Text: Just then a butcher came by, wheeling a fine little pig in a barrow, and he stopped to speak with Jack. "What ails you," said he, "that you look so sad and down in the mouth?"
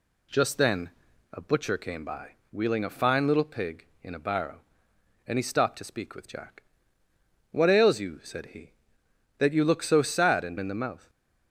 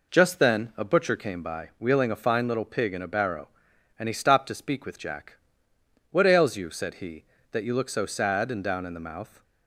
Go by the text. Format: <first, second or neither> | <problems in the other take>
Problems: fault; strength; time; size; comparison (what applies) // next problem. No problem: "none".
second | pauses between "then" and "a"; at 0.8 s; 0.44 s long // skips "down"; at 10.5 s